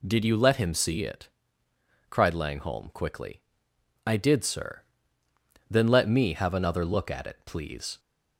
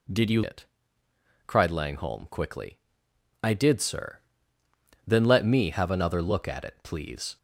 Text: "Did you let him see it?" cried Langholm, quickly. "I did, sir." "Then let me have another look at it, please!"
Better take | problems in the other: first | skips "let him see"; at 0.4 s

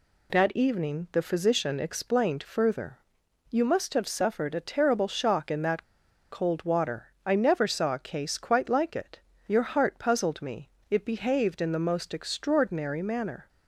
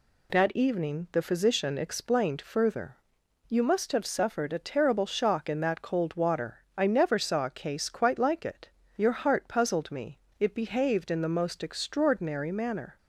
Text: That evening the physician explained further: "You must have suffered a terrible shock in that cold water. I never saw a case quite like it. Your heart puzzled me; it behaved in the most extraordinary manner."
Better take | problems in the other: second | pauses between "that" and "cold"; noticeable; at 5.8 s; 0.48 s long

